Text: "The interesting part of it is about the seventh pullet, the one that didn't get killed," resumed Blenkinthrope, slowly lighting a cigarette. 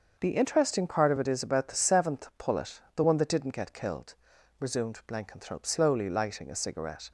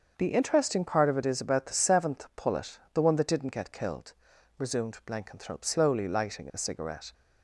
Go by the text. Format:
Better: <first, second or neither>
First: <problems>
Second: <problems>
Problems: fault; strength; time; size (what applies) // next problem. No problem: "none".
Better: neither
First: starts louder than the rest; until 1.2 s; 6.5 dB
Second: starts louder than the rest; until 1.1 s; 6.5 dB